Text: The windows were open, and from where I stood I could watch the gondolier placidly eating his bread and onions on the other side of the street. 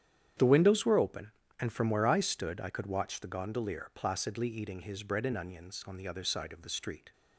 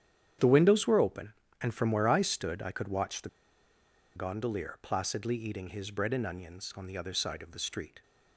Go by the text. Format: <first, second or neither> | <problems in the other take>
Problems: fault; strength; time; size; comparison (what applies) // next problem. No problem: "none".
first | starts louder than the rest; strong; until 1.6 s; 9.5 dB; strong in the first // pauses between "the" and "gondolier"; noticeable; at 3.2 s; 0.87 s long